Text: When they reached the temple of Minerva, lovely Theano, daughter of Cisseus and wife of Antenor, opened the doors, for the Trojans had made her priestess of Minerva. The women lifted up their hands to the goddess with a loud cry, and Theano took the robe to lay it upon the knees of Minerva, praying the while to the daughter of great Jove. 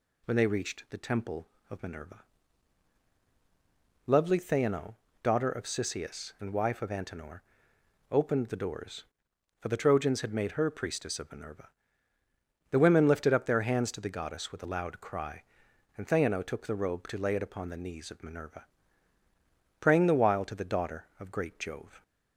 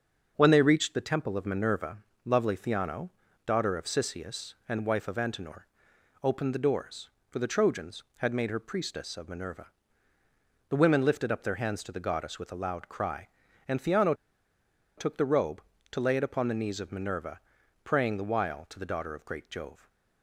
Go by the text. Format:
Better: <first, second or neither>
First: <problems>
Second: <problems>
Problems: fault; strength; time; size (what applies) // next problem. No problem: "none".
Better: first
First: none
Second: starts louder than the rest; until 1.3 s; 6.5 dB // pauses between "Theano" and "took"; noticeable; at 14.1 s; 0.83 s long